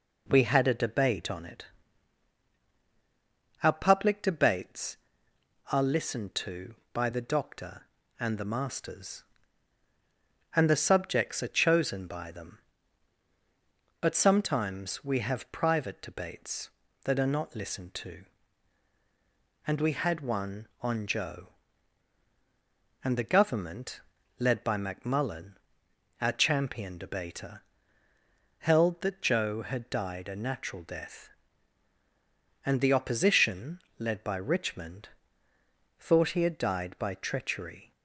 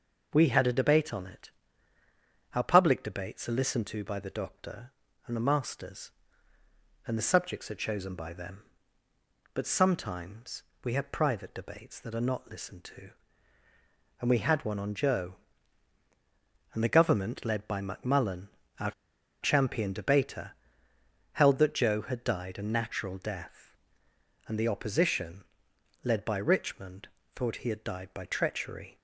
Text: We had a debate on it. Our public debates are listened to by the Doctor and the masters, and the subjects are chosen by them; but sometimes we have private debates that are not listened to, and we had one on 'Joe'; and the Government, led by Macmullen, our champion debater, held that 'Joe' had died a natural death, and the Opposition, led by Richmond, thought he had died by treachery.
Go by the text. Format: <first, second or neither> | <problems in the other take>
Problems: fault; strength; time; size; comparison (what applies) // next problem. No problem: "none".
first | pauses between "sometimes" and "we"; slight; at 10.6 s; 0.20 s long // pauses between "our" and "champion"; noticeable; at 18.9 s; 0.50 s long